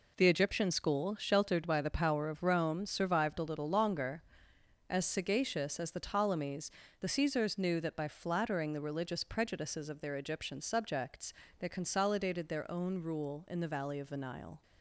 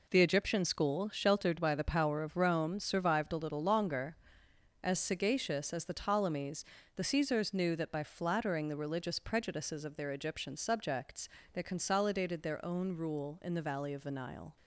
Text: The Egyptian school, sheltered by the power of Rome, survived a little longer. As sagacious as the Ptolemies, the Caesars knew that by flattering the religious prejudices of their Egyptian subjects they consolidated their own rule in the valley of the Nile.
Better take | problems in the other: neither | pauses between "subjects" and "they"; slight; the same in both

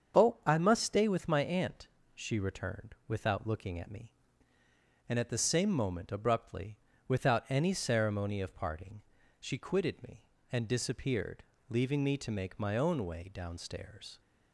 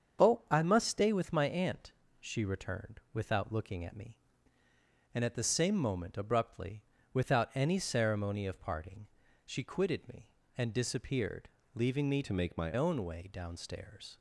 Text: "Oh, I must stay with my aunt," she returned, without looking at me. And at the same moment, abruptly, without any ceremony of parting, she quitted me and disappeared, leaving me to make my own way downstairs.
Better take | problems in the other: first | starts louder than the rest; until 1.3 s; 7 dB; also in the first // changes voice from "to" to "my"; from 12.2 to 12.7 s; 0.5 s long

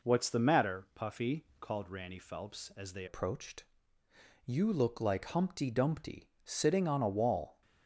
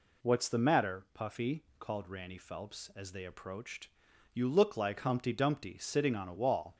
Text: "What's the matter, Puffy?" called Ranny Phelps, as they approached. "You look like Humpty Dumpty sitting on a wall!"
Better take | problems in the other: second | changes voice at "approached"; from 3.0 s on; 4.6 s long

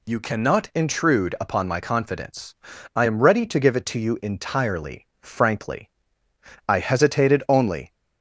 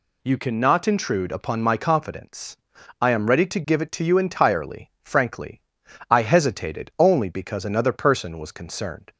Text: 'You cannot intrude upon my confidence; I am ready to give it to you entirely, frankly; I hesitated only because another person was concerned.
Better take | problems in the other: second | stops before "because another person was concerned"; at 7.9 s

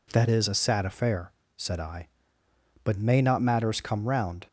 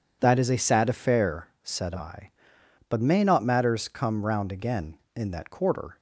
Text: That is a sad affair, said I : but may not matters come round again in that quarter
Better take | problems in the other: second | stops before "again in that quarter"; at 4.4 s

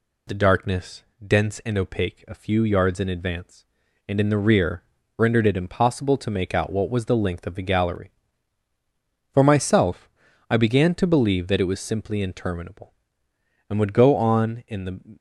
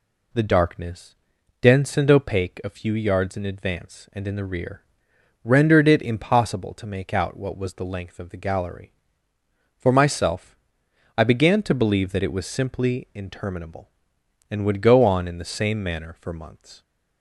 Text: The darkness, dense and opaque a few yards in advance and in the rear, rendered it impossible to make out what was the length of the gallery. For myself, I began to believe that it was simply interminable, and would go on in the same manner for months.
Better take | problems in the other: second | stops before "same manner for months"; at 15.1 s

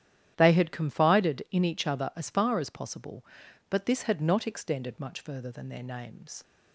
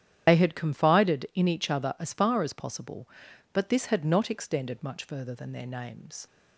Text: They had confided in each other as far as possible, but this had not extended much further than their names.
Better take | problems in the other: first | loses the start of "They"; at 0.2 s; 75 ms // starts louder than the rest; strong; until 1.3 s; 10 dB; strong in the first

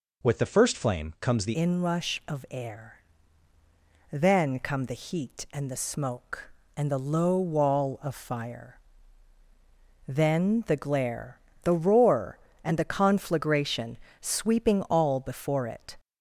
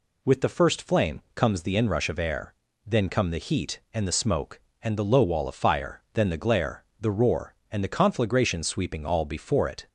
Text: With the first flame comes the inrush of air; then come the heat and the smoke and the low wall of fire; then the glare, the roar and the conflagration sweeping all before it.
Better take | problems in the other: second | changes voice at "inrush"; from 1.5 s on; 14.4 s long // pauses between "conflagration" and "sweeping"; slight; at 13.9 s; 0.24 s long

